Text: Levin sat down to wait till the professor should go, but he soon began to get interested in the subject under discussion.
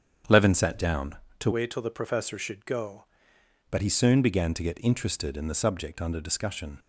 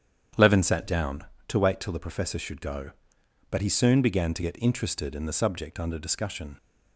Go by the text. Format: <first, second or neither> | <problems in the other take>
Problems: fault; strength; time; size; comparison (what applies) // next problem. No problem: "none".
second | starts louder than the rest; strong; until 1.5 s; 8 dB; strong in the second // changes voice from "wait" to "go"; from 1.5 to 3.0 s; 1.5 s long